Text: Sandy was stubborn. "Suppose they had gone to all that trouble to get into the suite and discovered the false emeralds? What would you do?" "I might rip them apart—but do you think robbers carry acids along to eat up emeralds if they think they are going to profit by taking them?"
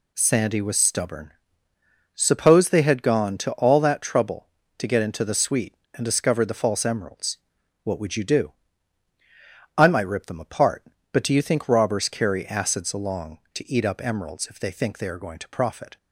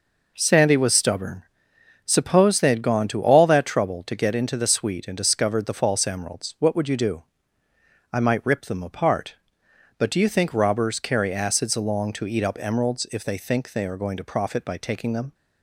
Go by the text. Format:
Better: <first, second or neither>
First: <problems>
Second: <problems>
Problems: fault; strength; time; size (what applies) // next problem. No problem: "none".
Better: second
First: stops before "by taking them"; at 15.9 s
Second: none